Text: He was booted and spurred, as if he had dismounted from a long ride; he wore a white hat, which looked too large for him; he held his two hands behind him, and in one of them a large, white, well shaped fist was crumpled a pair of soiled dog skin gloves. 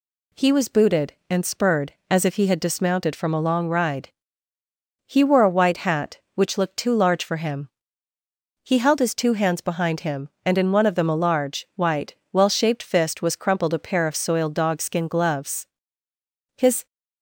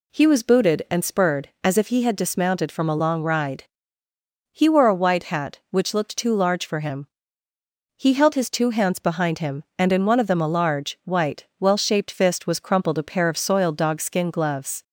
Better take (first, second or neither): second